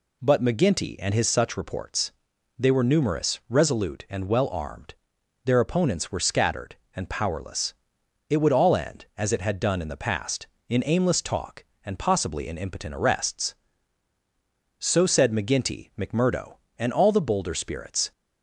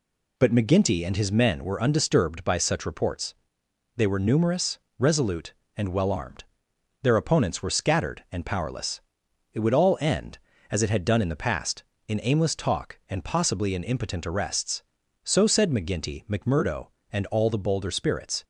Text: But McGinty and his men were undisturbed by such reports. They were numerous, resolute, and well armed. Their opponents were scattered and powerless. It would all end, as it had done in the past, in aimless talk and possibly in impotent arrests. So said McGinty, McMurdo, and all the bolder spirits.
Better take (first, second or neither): second